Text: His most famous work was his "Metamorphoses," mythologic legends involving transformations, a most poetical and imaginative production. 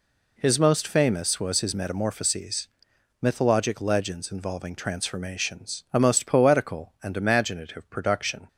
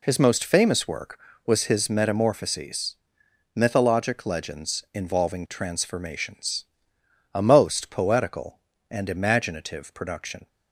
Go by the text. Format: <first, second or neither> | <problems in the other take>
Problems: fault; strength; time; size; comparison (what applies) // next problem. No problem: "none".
second | skips "work"; at 1.3 s